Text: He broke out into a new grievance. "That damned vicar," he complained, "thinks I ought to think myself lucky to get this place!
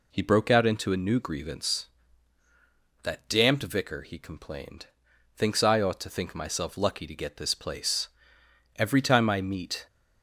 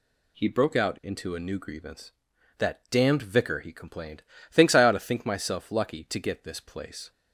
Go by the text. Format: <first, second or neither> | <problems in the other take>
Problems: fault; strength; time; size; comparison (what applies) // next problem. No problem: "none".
second | goes on to say "Every time I meet"; noticeable; from 8.7 s on; 1.1 s long